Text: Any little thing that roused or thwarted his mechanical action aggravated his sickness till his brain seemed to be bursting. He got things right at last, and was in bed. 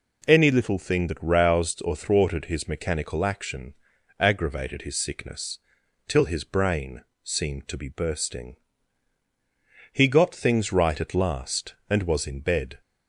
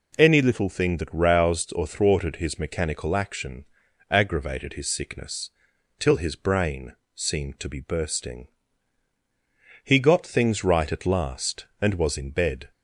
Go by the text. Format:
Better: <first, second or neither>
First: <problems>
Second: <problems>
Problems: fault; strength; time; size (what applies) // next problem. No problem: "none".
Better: neither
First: pauses between "action" and "aggravated"; noticeable; at 3.7 s; 0.46 s long // pauses between "sickness" and "till"; noticeable; at 5.5 s; 0.48 s long // pauses between "brain" and "seemed"; slight; at 7.0 s; 0.20 s long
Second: pauses between "action" and "aggravated"; noticeable; at 3.6 s; 0.46 s long // pauses between "sickness" and "till"; noticeable; at 5.4 s; 0.48 s long // pauses between "brain" and "seemed"; slight; at 6.9 s; 0.20 s long